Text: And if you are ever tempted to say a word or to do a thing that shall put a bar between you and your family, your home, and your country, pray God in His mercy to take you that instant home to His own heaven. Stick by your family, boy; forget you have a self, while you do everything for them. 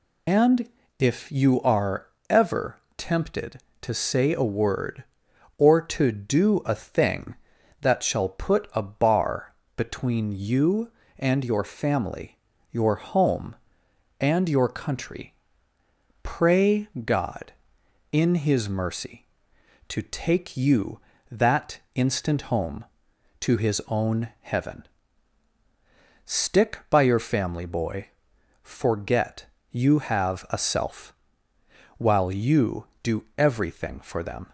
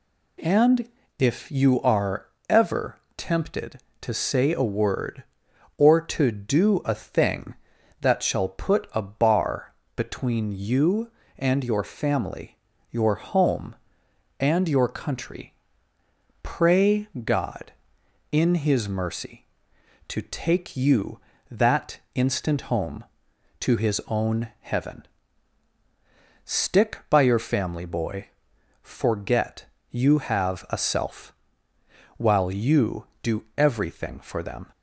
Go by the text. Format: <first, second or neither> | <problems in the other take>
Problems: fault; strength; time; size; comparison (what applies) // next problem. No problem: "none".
second | loses the start of "And"; at 0.2 s; 90 ms // pauses between "And" and "if"; slight; at 0.6 s; 0.32 s long; slight in the second // pauses between "are" and "ever"; slight; at 2.0 s; 0.22 s long; slight in the second // pauses between "ever" and "tempted"; slight; at 2.7 s; 0.20 s long; slight in the second // pauses between "bar" and "between"; slight; at 9.5 s; 0.22 s long; slight in the second // pauses between "pray" and "God"; slight; at 16.8 s; 0.16 s long; slight in the second // pauses between "that" and "instant"; slight; at 21.7 s; 0.16 s long; slight in the second // pauses between "forget" and "you"; slight; at 29.4 s; 0.26 s long; slight in the second